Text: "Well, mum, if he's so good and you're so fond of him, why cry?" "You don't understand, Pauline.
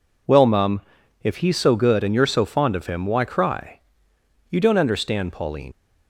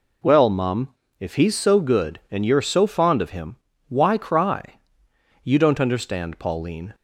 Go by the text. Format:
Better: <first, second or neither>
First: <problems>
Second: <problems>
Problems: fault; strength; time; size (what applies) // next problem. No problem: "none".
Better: second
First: leaves "Pauline" unfinished; at 5.7 s; 60 ms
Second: none